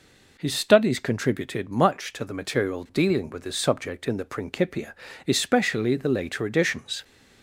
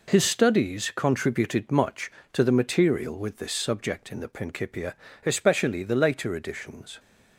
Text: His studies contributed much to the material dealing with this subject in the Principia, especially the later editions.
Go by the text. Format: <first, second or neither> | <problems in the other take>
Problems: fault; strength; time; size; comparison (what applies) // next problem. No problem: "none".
first | skips "dealing"; at 3.1 s